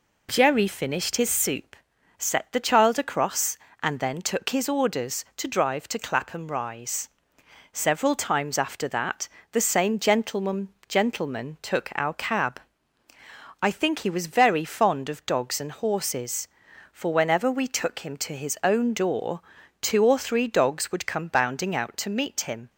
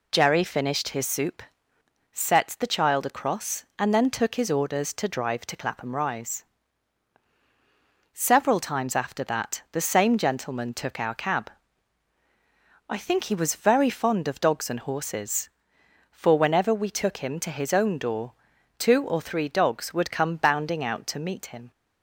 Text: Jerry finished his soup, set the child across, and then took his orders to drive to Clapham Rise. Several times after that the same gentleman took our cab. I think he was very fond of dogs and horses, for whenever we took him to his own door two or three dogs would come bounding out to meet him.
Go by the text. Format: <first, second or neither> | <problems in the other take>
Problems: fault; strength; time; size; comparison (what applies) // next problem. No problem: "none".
second | pauses between "that" and "the"; slight; at 9.2 s; 0.26 s long // says "gentleman" twice; at 10.8 s // pauses between "door" and "two"; at 19.3 s; 0.42 s long; noticeable in the second